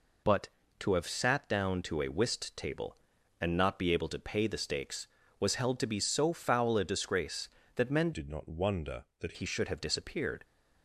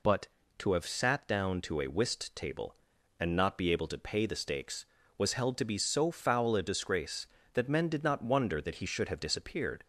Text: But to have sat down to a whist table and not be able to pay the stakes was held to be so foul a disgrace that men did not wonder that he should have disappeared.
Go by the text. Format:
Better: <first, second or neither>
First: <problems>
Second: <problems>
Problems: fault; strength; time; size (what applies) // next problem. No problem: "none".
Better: second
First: changes voice from "did" to "that"; from 8.1 to 9.3 s; 1.2 s long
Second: none